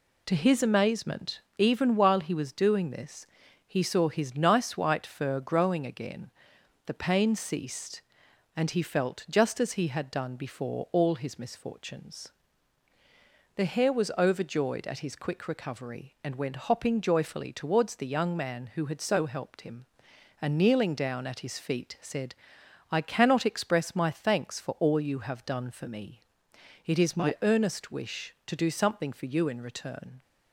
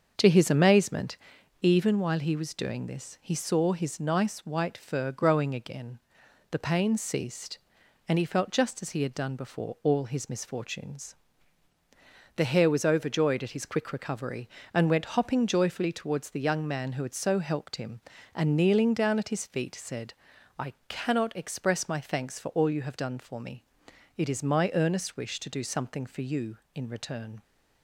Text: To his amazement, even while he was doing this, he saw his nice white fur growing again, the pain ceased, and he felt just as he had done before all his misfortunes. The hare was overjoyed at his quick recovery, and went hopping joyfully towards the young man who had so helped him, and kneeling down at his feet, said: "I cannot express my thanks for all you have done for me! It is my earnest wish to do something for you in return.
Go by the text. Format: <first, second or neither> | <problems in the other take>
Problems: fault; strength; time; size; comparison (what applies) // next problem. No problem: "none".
first | starts louder than the rest; until 1.5 s; 6.5 dB // pauses between "I" and "cannot"; slight; at 20.7 s; 0.16 s long